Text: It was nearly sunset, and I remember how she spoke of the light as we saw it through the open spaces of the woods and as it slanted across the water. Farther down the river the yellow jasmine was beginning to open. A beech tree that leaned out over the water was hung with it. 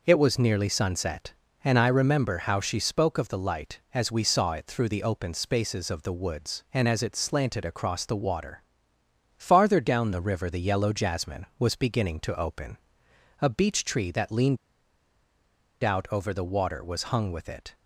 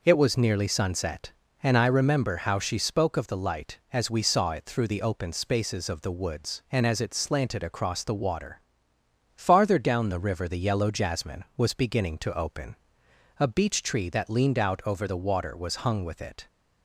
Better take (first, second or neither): second